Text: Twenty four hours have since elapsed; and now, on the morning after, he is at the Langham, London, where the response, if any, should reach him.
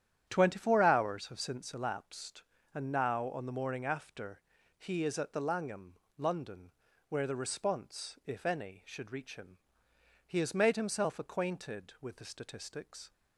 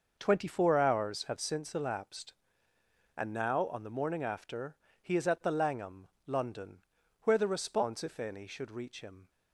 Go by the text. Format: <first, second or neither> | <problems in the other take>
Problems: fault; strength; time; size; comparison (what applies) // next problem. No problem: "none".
second | starts louder than the rest; strong; until 1.2 s; 10 dB // goes on to say "He has made himself acquainted with the statistics"; strong; from 10.2 s on; 2.8 s long